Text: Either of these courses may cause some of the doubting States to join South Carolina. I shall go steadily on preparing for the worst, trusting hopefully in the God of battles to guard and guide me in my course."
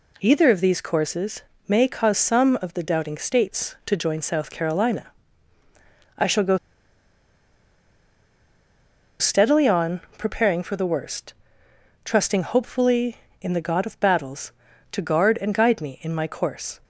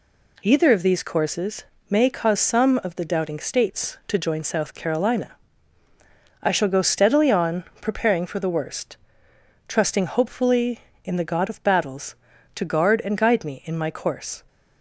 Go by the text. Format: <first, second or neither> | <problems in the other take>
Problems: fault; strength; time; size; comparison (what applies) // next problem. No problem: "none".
second | pauses between "courses" and "may"; slight; at 1.4 s; 0.26 s long; slight in the second // pauses between "go" and "steadily"; strong; at 6.5 s; 2.6 s long // pauses between "on" and "preparing"; slight; at 10.0 s; 0.18 s long; slight in the second